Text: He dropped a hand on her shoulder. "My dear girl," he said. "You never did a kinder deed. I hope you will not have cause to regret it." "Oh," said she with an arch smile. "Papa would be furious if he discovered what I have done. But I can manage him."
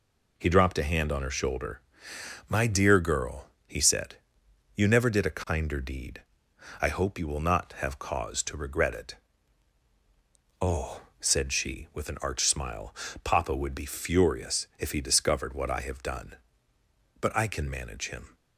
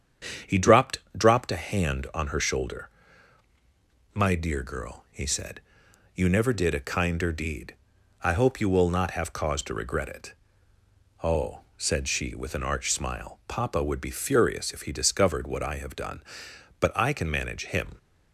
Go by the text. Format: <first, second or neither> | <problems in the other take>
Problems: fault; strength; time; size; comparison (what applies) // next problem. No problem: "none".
first | starts louder than the rest; strong; until 1.6 s; 8 dB // says "dropped" twice; at 1.1 s